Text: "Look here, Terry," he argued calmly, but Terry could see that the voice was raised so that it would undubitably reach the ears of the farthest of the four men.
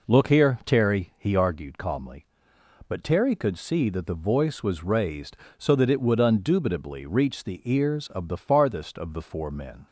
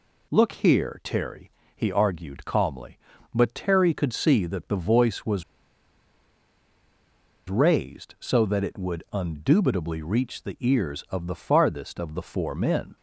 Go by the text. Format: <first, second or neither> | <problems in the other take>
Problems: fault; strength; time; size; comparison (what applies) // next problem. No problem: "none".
first | pauses between "was" and "raised"; strong; at 5.4 s; 2.0 s long